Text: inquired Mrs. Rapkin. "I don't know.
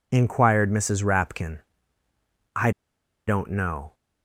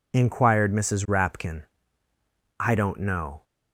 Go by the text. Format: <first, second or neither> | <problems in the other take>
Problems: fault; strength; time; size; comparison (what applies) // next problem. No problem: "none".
second | pauses between "I" and "don't"; noticeable; at 2.7 s; 0.56 s long